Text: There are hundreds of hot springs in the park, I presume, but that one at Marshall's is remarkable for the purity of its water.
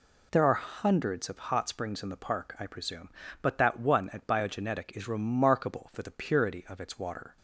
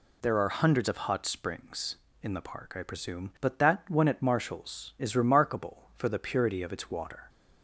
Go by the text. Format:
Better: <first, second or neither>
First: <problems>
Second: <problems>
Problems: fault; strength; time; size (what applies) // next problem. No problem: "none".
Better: second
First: says "Biogenetic" for "Marshall's"; at 4.2 s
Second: none